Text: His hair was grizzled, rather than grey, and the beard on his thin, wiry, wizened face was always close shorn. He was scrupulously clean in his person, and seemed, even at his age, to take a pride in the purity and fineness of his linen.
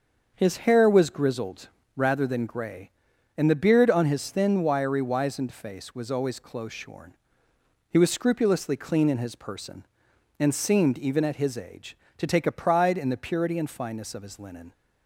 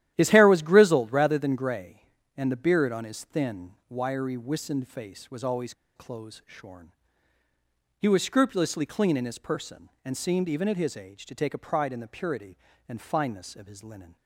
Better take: first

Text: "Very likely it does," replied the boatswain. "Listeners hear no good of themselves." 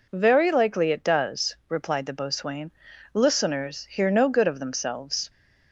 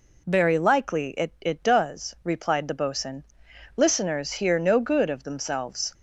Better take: first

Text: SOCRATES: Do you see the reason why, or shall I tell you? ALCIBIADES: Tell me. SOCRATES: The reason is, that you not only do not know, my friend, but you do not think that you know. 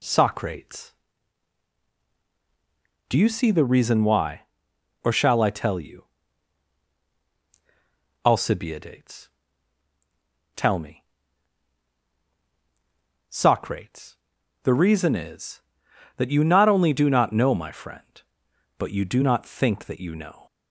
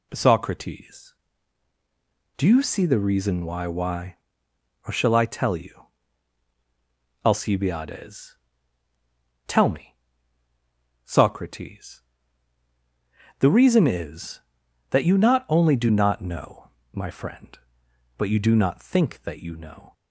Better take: first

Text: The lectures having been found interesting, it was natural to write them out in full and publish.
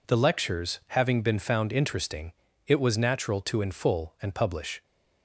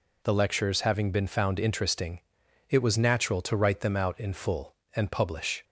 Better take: second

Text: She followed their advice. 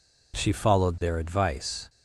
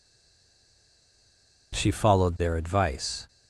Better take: first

